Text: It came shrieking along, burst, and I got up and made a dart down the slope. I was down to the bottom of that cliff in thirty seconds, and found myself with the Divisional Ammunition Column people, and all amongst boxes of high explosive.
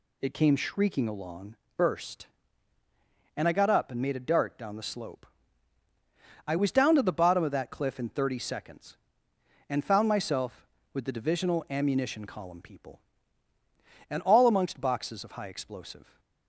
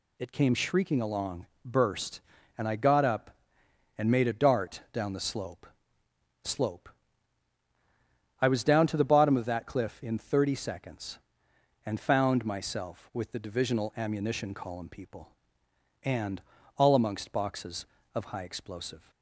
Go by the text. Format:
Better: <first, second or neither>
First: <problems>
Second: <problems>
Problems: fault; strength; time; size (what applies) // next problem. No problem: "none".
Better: first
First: none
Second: says "slope" twice; at 6.4 s // pauses between "and" and "all"; at 16.4 s; 0.38 s long